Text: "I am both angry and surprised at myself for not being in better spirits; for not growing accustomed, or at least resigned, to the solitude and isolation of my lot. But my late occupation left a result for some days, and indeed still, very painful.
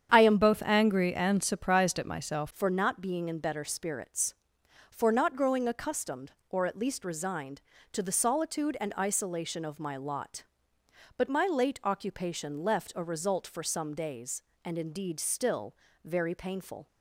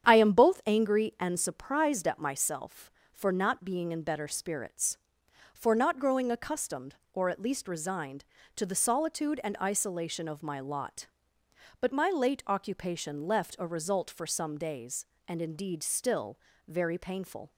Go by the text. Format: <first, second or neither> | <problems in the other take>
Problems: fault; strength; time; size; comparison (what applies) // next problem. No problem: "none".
second | starts louder than the rest; strong; until 1.1 s; 8.5 dB; strong in the second // changes voice from "both" to "myself"; from 0.4 to 2.4 s; 2.0 s long